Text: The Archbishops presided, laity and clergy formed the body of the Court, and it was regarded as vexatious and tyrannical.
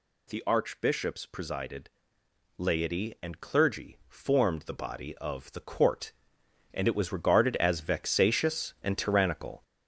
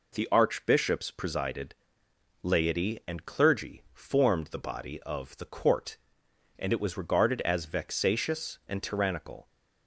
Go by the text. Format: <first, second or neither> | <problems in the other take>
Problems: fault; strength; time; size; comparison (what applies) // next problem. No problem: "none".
second | gets louder; noticeable; throughout; 5.5 dB